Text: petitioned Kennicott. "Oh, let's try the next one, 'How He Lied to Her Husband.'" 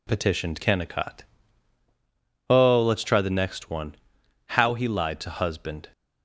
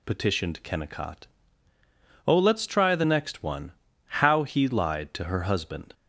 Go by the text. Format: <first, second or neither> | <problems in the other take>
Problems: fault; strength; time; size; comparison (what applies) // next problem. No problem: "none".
second | skips "Her"; at 5.3 s